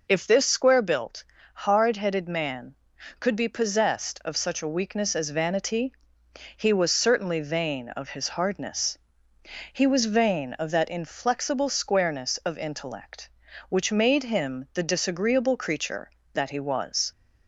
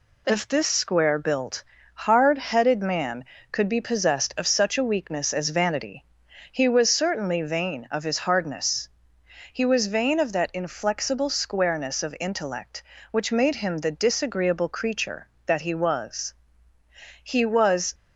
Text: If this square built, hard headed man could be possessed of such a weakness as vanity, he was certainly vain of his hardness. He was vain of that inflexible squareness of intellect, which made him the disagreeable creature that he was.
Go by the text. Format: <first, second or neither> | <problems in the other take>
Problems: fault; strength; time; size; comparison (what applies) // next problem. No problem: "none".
first | goes on to say "He was"; noticeable; from 17.2 s on; 0.72 s long